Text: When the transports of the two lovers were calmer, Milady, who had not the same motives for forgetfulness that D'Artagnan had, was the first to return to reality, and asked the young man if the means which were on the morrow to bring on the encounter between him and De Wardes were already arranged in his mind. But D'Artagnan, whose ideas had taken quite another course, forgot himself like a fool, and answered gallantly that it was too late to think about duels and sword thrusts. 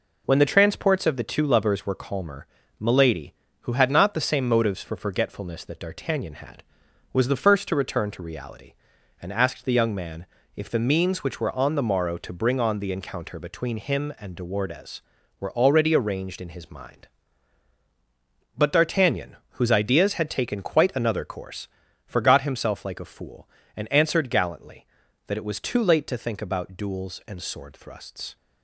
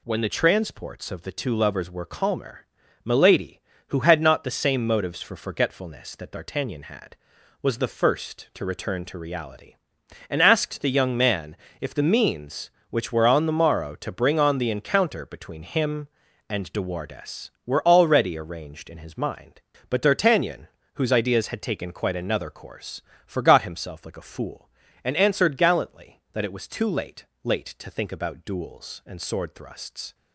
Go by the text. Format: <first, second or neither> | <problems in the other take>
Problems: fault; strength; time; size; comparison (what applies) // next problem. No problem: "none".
first | pauses between "man" and "if"; slight; at 11.5 s; 0.24 s long; slight in the first // says "late" twice; at 27.4 s